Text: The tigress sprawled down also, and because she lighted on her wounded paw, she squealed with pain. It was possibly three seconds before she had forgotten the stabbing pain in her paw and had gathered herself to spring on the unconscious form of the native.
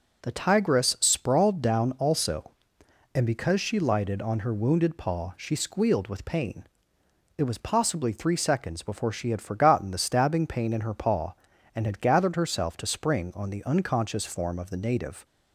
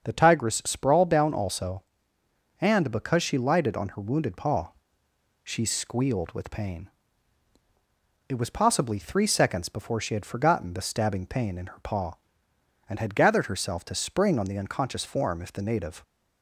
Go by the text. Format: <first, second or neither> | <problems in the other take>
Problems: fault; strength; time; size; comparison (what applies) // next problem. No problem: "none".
first | starts louder than the rest; until 1.0 s; 7 dB // says "if" for "of"; at 15.4 s